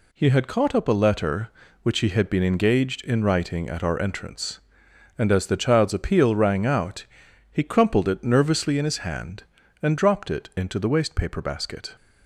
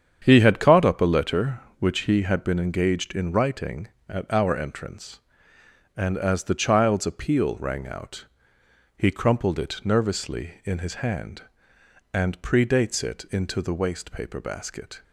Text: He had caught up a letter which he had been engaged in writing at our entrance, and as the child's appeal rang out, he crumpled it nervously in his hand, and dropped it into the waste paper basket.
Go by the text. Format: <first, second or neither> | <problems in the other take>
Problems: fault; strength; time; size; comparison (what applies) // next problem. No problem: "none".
first | starts louder than the rest; strong; until 1.2 s; 8 dB // says "predates" for "dropped"; at 12.4 s